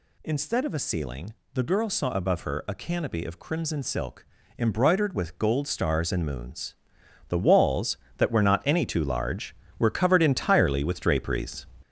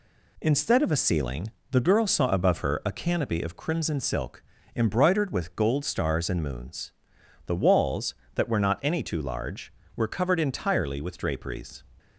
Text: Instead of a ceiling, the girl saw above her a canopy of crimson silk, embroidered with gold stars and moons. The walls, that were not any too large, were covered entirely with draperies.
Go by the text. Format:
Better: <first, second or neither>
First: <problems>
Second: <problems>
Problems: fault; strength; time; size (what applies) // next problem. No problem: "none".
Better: second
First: gets louder; noticeable; throughout; 5.5 dB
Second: none